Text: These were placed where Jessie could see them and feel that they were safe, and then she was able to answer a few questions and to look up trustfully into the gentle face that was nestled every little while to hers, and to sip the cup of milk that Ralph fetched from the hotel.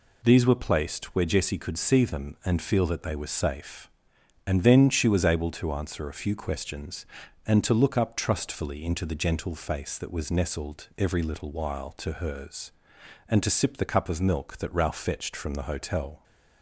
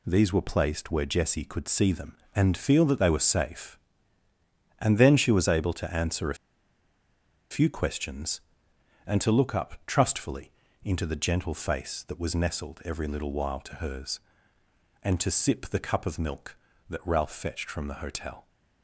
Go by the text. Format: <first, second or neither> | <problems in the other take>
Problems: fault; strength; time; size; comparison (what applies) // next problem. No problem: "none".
first | pauses between "a" and "few"; at 6.3 s; 1.1 s long // pauses between "trustfully" and "into"; slight; at 10.5 s; 0.32 s long